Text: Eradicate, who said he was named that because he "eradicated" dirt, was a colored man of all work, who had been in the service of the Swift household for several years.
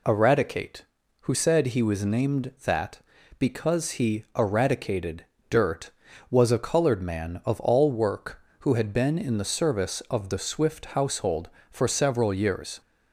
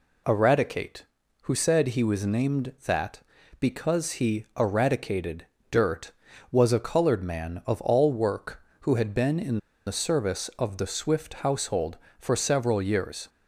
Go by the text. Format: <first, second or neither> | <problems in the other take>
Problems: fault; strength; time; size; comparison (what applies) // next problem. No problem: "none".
first | pauses between "eradicated" and "dirt"; slight; at 5.4 s; 0.26 s long; slight in the first // pauses between "in" and "the"; slight; at 9.5 s; 0.28 s long